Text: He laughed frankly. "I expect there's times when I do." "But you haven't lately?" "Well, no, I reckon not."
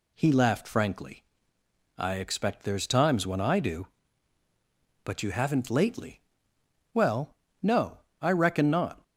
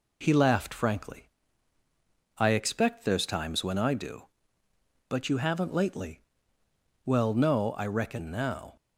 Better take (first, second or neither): first